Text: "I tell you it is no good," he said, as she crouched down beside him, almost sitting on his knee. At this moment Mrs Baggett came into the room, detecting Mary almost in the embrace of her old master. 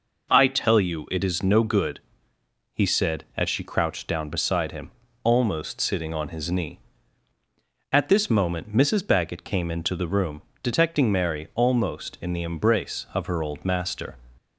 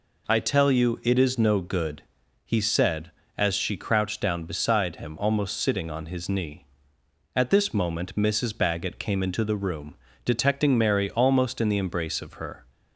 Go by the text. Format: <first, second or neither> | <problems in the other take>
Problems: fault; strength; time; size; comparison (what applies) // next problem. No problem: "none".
first | stops before "old master"; at 12.6 s